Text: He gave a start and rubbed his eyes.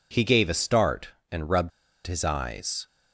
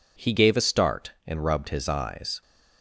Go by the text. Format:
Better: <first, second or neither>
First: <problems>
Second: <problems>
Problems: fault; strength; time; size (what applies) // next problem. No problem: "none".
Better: second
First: pauses between "rubbed" and "his"; slight; at 1.7 s; 0.35 s long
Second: none